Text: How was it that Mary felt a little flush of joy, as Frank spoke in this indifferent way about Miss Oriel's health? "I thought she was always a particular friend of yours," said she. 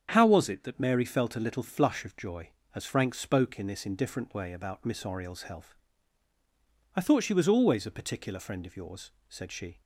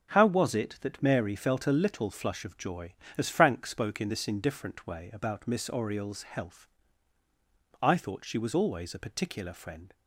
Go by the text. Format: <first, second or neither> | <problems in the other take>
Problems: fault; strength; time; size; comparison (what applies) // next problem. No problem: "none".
first | starts louder than the rest; until 1.1 s; 7 dB; strong in the first // stops before "of yours said she"; at 9.9 s